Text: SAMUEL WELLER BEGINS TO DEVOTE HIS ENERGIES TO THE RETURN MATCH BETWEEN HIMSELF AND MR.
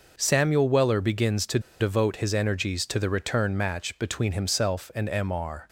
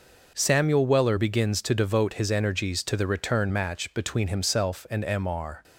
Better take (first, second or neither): second